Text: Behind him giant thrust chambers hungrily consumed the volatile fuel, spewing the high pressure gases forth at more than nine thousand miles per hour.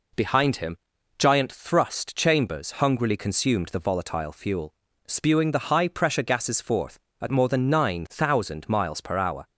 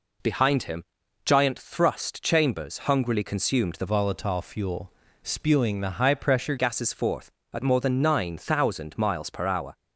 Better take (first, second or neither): first